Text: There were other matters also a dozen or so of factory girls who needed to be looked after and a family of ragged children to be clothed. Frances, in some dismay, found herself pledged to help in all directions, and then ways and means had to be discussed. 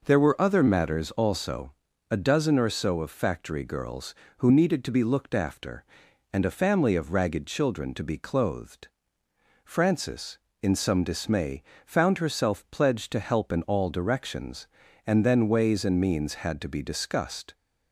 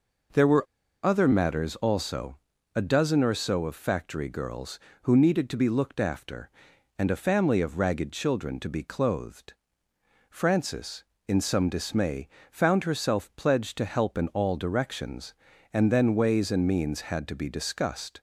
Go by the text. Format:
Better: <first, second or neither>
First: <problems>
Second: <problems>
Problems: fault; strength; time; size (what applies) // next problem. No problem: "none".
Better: first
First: pauses between "also" and "a"; at 1.7 s; 0.40 s long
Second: pauses between "were" and "other"; at 0.6 s; 0.38 s long // pauses between "also" and "a"; at 2.3 s; 0.40 s long